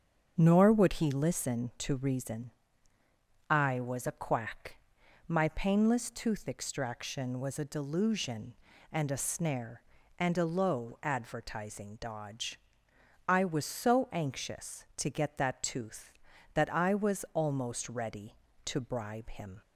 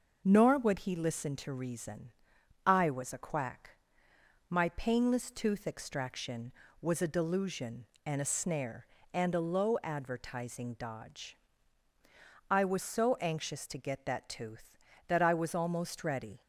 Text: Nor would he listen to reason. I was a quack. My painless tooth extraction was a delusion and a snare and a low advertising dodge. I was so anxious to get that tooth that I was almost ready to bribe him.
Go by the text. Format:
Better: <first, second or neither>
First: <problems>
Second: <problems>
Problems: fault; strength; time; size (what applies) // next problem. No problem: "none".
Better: first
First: starts louder than the rest; until 1.3 s; 7 dB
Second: starts louder than the rest; noticeable; until 1.2 s; 6 dB // stops before "to bribe him"; at 16.4 s